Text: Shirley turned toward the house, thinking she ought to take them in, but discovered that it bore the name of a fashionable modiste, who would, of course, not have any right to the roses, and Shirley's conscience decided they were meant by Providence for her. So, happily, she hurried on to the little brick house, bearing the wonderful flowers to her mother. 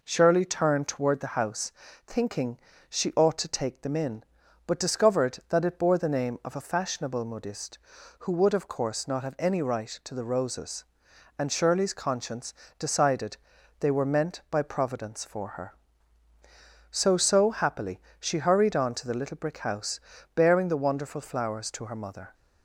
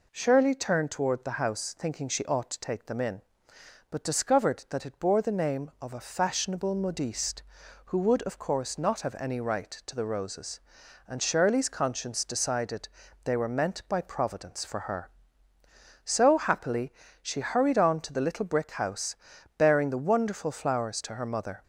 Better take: second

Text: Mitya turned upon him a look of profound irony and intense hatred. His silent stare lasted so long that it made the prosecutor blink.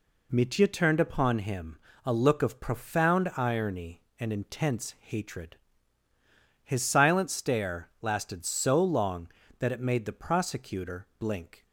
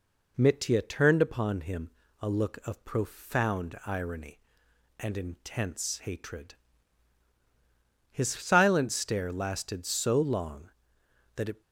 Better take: first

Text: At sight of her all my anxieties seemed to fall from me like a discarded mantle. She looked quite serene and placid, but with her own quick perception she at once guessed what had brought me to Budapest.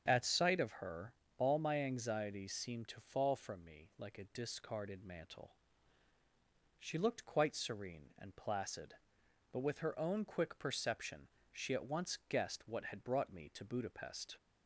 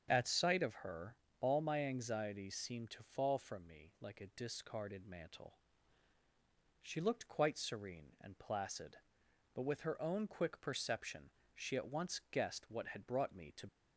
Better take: first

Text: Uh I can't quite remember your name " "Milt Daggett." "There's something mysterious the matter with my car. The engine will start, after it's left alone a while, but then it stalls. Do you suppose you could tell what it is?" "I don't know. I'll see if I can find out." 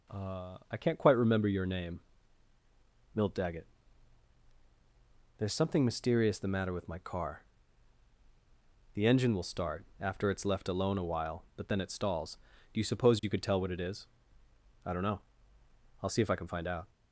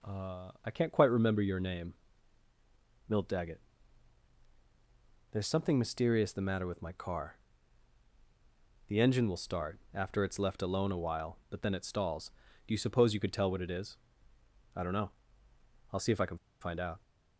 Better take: first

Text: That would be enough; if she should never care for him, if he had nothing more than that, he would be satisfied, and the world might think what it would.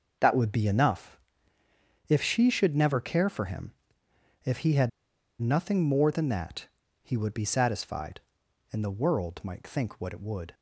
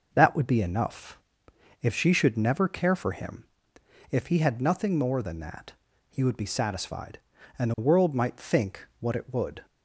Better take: second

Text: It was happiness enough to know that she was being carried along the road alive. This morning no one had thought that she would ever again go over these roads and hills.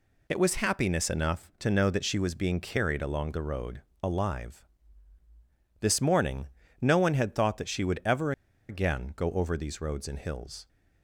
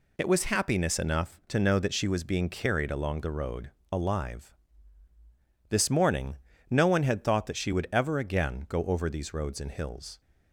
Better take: second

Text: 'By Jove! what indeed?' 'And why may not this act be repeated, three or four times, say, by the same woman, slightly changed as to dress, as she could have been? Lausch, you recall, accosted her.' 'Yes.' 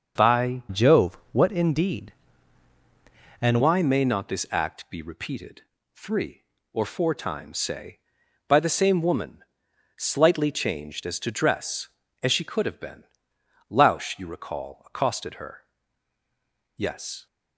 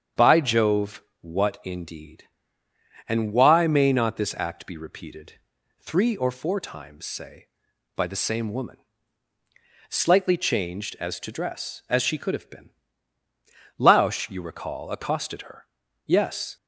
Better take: second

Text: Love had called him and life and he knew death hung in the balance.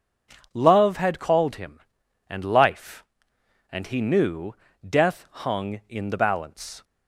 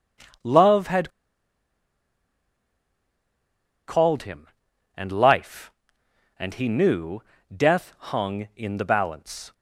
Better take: first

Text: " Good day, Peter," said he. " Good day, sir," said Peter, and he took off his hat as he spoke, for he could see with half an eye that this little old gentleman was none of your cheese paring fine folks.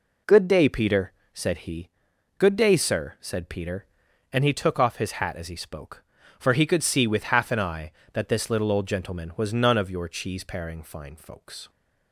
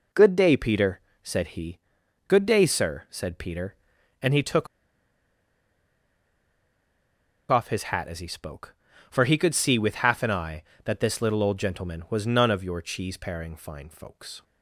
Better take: first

